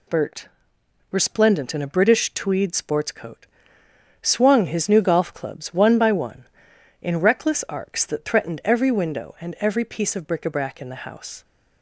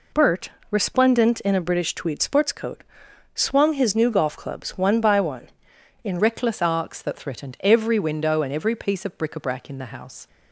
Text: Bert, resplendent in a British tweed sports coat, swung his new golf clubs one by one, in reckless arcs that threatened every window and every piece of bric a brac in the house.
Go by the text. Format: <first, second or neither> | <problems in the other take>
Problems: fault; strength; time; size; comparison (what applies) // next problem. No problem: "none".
first | changes voice at "reckless"; from 6.1 s on; 4.1 s long